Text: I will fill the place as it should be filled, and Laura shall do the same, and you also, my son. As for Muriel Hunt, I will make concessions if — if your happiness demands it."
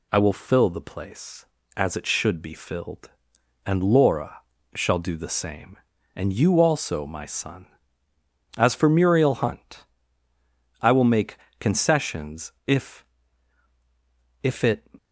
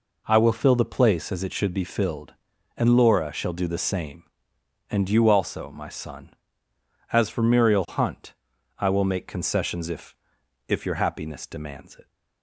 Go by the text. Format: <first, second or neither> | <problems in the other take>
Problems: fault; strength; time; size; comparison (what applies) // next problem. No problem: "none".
second | pauses between "Laura" and "shall"; slight; at 4.4 s; 0.34 s long // pauses between "make" and "concessions"; slight; at 11.3 s; 0.22 s long // skips "your happiness demands"; at 14.6 s